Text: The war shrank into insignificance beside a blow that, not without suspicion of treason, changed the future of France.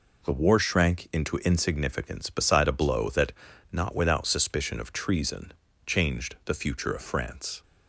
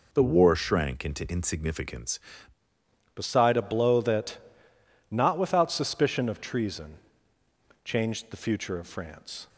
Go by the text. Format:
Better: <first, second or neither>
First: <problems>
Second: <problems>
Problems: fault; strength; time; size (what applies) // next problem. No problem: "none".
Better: first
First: none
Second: changes voice at "beside"; from 3.1 s on; 6.3 s long